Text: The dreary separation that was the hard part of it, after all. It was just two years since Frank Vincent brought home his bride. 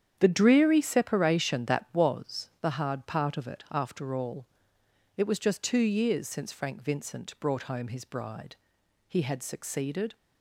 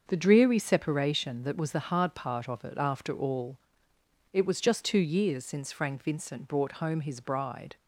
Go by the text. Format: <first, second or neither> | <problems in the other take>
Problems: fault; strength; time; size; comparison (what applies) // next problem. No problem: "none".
second | starts louder than the rest; strong; until 1.2 s; 9 dB; also in the second // goes on to say "He had succeeded"; noticeable; from 9.0 s on; 1.0 s long